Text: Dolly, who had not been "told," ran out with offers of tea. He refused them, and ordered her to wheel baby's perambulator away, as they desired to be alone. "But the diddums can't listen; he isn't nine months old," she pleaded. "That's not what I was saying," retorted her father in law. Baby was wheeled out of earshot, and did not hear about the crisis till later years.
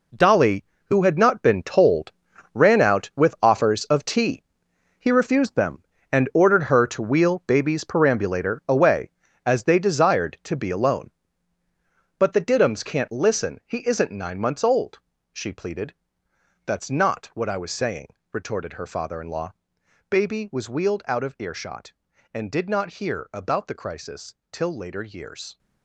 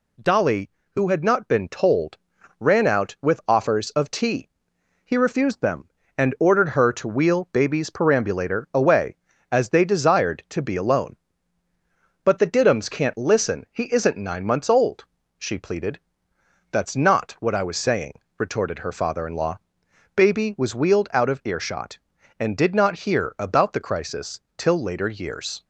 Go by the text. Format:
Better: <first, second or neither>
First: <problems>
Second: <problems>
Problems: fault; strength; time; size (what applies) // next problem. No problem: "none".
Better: second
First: gets quieter; strong; throughout; 10.5 dB // pauses between "crisis" and "till"; slight; at 24.3 s; 0.16 s long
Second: pauses between "crisis" and "till"; slight; at 24.4 s; 0.16 s long